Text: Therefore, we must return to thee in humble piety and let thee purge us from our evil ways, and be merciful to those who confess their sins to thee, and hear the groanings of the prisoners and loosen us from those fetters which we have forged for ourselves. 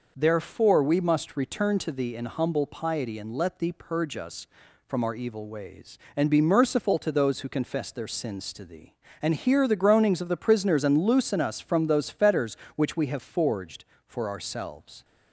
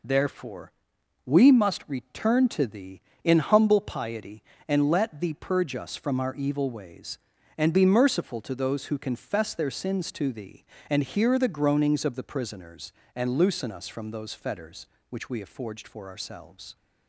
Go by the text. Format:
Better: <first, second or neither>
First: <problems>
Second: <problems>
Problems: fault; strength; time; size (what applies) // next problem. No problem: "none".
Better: neither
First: none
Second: none